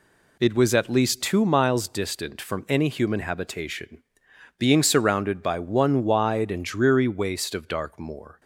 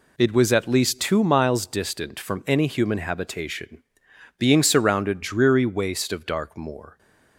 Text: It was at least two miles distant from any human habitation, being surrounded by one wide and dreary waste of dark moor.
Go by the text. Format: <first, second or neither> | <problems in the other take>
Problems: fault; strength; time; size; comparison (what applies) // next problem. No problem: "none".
first | skips "by one wide and"; at 5.2 s